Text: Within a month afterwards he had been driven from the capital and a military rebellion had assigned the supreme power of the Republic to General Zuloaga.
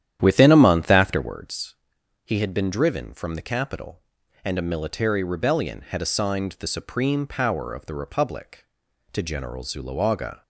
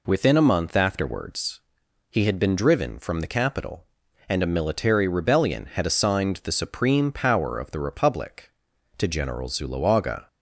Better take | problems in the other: second | starts louder than the rest; strong; until 1.3 s; 10.5 dB // pauses between "afterwards" and "he"; noticeable; at 1.7 s; 0.52 s long; noticeable in the second

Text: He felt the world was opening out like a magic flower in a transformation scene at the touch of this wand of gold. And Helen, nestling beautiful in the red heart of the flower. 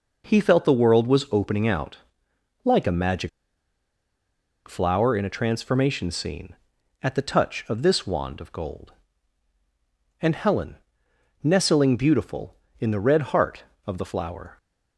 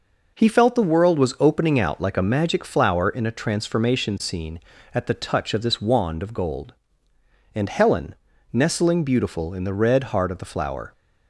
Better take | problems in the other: second | pauses between "out" and "like"; noticeable; at 1.9 s; 0.66 s long // pauses between "magic" and "flower"; strong; at 3.2 s; 1.3 s long

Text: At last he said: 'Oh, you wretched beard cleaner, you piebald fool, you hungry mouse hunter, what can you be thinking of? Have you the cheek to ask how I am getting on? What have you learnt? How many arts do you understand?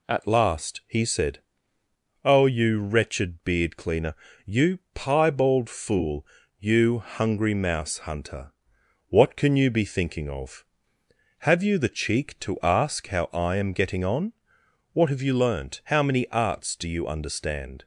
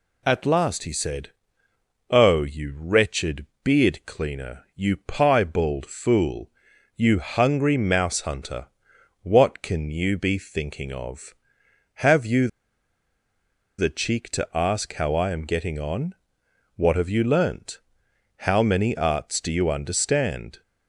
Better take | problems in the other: first | pauses between "wretched" and "beard"; slight; at 3.4 s; 0.20 s long // pauses between "you" and "the"; strong; at 12.4 s; 1.3 s long

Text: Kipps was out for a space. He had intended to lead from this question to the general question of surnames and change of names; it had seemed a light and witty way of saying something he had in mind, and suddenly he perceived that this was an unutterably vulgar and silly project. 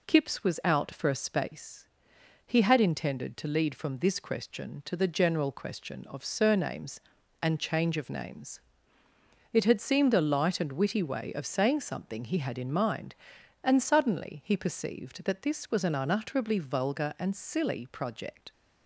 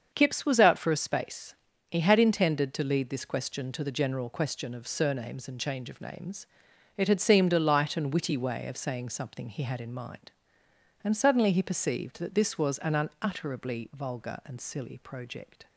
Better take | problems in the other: first | starts louder than the rest; until 1.1 s; 7 dB // skips "from"; at 3.0 s

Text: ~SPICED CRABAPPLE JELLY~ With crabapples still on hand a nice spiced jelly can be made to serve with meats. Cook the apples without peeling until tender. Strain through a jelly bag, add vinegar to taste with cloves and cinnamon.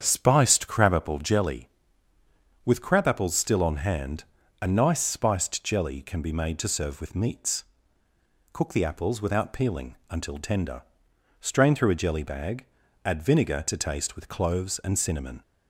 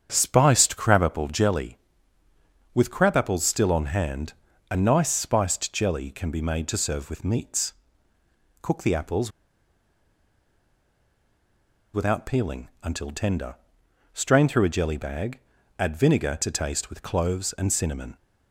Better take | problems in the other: first | starts louder than the rest; strong; until 1.1 s; 8 dB; strong in the first // pauses between "hand" and "a"; slight; at 4.3 s; 0.36 s long; slight in the first // pauses between "apples" and "without"; strong; at 9.3 s; 2.6 s long

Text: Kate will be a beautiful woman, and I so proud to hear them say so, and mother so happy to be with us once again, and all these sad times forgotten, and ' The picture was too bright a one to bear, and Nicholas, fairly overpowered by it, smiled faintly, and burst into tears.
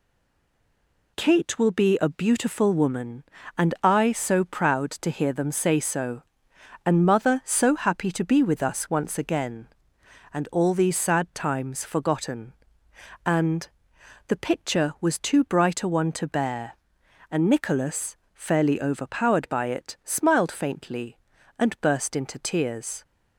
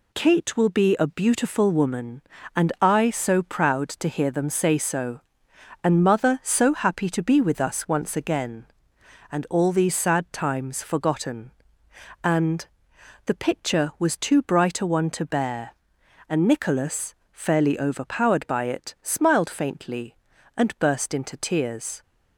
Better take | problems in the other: second | stays silent before the first word; until 1.1 s; 1.1 s long

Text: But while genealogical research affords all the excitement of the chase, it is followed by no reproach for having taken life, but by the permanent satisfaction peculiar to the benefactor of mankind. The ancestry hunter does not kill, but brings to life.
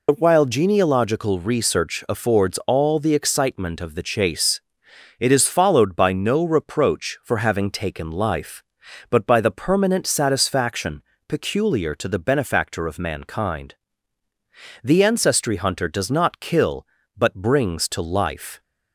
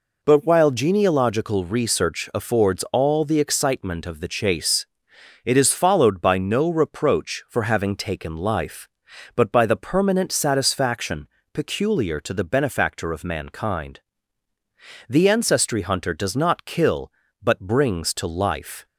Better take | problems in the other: second | loses the start of "But"; at 0.0 s; 105 ms // pauses between "satisfaction" and "peculiar"; slight; at 11.0 s; 0.26 s long; slight in the second

